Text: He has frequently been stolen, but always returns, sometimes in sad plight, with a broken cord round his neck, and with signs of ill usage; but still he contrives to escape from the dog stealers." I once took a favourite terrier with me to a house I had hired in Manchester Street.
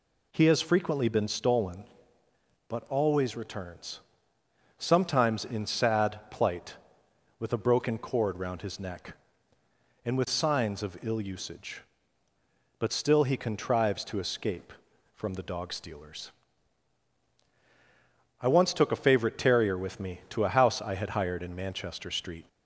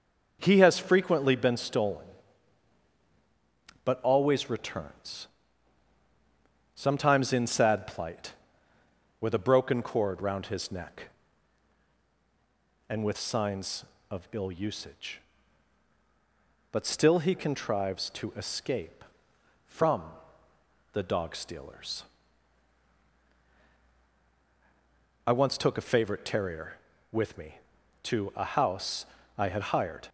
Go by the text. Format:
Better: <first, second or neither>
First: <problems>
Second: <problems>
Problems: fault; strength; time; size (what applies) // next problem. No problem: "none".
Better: first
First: none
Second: starts louder than the rest; noticeable; until 1.4 s; 6 dB // pauses between "from" and "the"; noticeable; at 20.0 s; 0.88 s long // pauses between "house" and "I"; slight; at 29.0 s; 0.32 s long // stops before "in Manchester Street"; at 30.0 s